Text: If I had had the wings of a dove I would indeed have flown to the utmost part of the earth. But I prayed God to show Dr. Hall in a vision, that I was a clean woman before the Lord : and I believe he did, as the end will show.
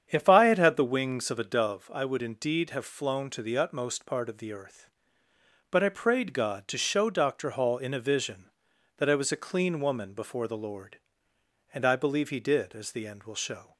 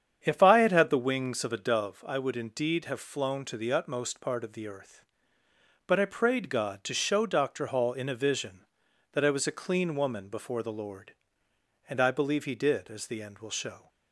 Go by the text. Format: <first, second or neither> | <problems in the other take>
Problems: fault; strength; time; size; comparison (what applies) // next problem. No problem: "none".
neither | starts louder than the rest; strong; the same in both